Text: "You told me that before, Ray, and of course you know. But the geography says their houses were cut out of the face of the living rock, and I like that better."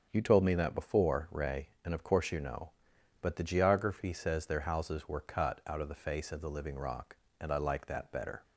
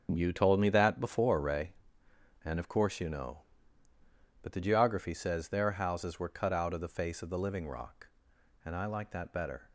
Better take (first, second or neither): neither